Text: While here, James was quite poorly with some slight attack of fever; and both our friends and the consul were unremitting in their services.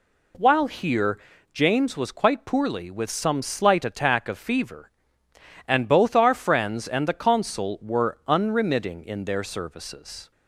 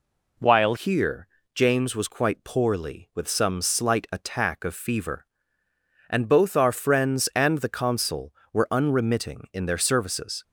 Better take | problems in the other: first | changes voice at "here"; from 0.7 s on; 9.7 s long

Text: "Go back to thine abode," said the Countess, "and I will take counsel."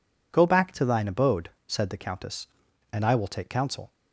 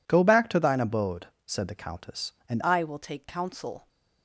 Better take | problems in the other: first | changes voice at "I"; from 2.6 s on; 1.2 s long

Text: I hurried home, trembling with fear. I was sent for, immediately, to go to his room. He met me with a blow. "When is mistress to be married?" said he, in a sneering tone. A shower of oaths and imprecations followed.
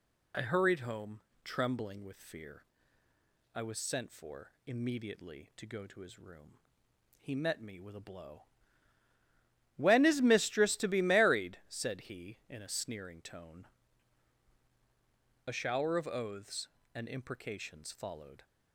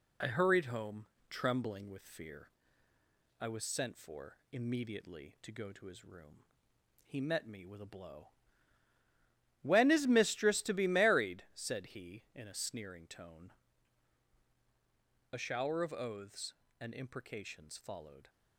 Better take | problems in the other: first | gets quieter; slight; throughout; 2.5 dB

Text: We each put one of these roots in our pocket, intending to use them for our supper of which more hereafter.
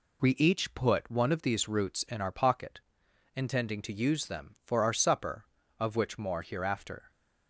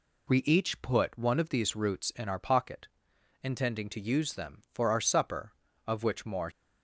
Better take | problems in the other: first | stops before "hereafter"; at 6.5 s

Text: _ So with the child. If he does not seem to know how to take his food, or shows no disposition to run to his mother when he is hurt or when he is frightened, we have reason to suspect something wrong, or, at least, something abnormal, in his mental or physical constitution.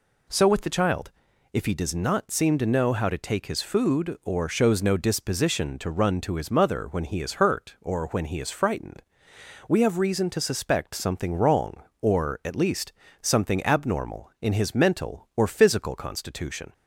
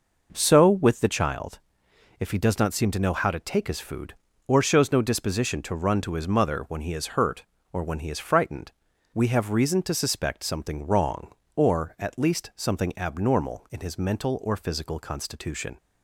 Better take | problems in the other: first | starts louder than the rest; noticeable; until 1.3 s; 5.5 dB

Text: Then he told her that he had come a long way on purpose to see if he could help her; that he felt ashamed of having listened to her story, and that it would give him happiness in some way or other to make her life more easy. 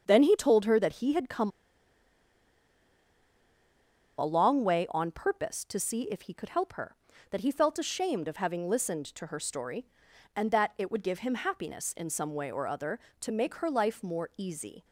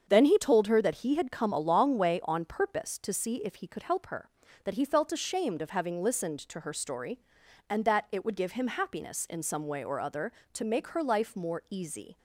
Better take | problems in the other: second | starts louder than the rest; strong; until 1.0 s; 7 dB; strong in the second // pauses between "come" and "a"; strong; at 1.5 s; 2.6 s long

